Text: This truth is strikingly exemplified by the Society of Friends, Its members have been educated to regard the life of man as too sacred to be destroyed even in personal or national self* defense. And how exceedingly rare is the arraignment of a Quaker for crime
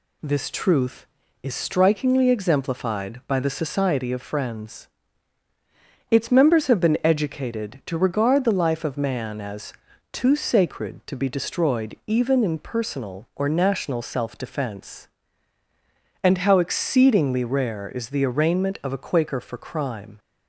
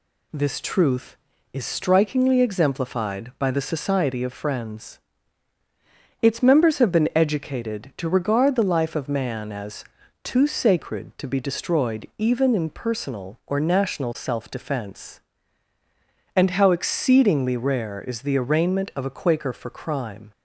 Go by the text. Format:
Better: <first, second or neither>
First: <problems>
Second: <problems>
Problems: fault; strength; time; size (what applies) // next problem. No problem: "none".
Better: neither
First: pauses between "as" and "too"; at 9.7 s; 0.40 s long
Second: pauses between "as" and "too"; at 9.8 s; 0.40 s long